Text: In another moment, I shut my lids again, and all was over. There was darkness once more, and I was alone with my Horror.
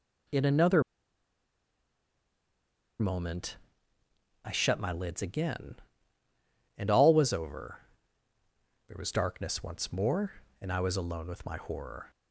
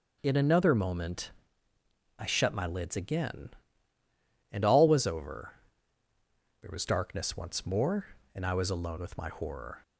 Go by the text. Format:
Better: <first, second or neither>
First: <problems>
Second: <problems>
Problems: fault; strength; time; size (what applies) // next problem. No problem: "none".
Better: second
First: pauses between "another" and "moment"; strong; at 0.8 s; 2.1 s long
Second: none